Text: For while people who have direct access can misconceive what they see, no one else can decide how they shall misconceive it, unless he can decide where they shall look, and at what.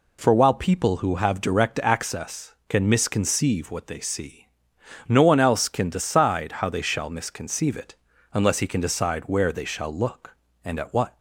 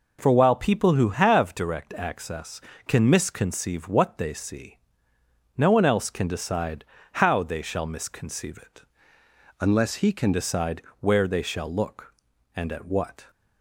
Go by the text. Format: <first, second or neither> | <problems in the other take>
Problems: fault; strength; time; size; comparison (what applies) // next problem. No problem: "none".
first | pauses between "decide" and "how"; slight; at 6.8 s; 0.30 s long // changes voice from "unless" to "can"; from 9.6 to 10.3 s; 0.7 s long // pauses between "decide" and "where"; slight; at 10.8 s; 0.18 s long